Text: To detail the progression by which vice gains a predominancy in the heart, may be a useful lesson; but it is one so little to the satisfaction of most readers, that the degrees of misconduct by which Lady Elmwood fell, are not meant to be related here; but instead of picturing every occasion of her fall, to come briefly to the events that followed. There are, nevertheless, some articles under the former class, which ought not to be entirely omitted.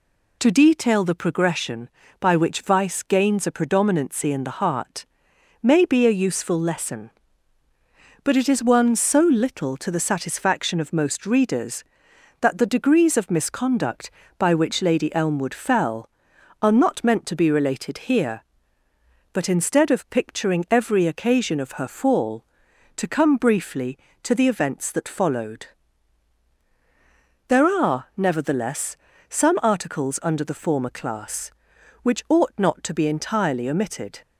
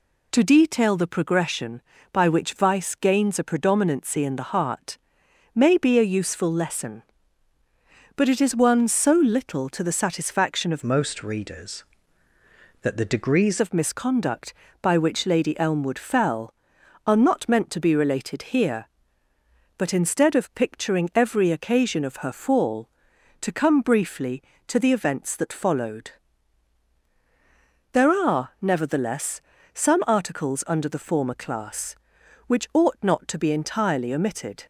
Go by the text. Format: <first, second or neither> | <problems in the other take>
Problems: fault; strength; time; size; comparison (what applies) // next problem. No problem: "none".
first | changes voice from "most" to "degrees"; from 10.8 to 13.6 s; 2.8 s long